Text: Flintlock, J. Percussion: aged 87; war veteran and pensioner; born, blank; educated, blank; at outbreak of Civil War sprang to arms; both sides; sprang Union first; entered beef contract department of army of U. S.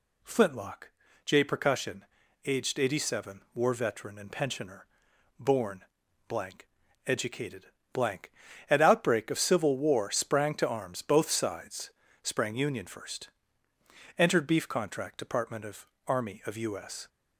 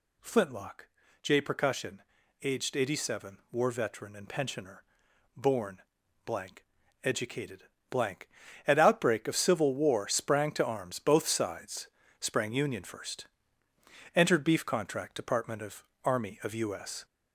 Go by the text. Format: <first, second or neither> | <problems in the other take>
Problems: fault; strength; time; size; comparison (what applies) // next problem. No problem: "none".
first | gets louder; slight; throughout; 2.5 dB // pauses between "of" and "army"; slight; at 15.8 s; 0.20 s long; slight in the first